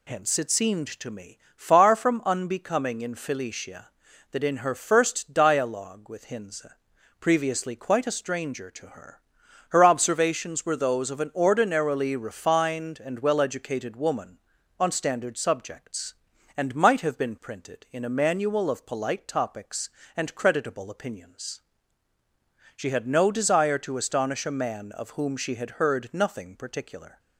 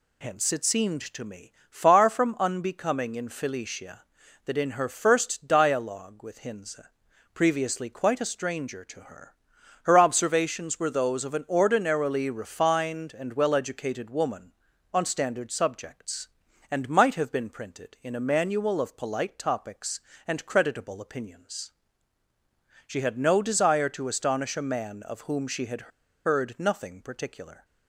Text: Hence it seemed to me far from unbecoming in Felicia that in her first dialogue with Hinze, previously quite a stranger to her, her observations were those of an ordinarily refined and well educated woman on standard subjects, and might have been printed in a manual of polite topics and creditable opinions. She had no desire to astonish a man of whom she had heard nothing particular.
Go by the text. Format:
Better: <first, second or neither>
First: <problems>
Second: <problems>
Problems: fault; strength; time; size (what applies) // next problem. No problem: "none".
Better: first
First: pauses between "me" and "far"; slight; at 1.3 s; 0.16 s long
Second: pauses between "me" and "far"; slight; at 1.5 s; 0.16 s long // pauses between "had" and "heard"; slight; at 25.8 s; 0.35 s long